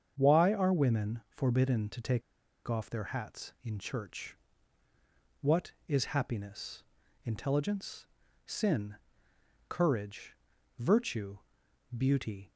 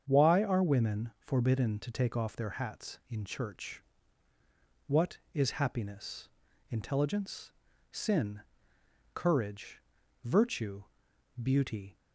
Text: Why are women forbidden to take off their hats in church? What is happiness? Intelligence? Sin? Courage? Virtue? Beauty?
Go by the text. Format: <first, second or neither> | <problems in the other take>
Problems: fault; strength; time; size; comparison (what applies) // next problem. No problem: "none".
second | starts louder than the rest; strong; until 1.1 s; 7.5 dB; strong in the second // pauses between "take" and "off"; noticeable; at 2.2 s; 0.46 s long